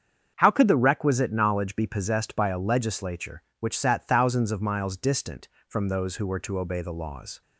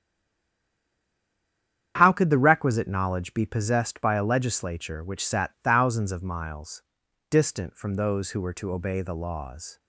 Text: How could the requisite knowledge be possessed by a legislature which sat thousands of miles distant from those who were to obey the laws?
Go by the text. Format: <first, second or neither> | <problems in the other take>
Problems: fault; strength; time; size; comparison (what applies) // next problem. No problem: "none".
first | stays silent before the first word; noticeable; until 1.9 s; 1.9 s long // starts louder than the rest; strong; until 2.9 s; 9 dB; strong in the first // pauses between "miles" and "distant"; noticeable; at 6.8 s; 0.48 s long